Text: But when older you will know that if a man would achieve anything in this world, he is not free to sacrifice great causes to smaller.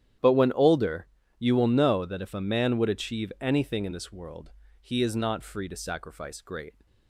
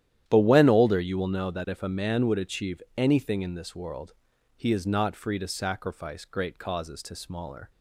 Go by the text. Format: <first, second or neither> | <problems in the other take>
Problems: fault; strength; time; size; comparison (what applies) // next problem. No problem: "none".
second | starts louder than the rest; strong; until 1.5 s; 11 dB; strong in the second // pauses between "older" and "you"; slight; at 1.0 s; 0.34 s long // stops before "causes to smaller"; at 6.8 s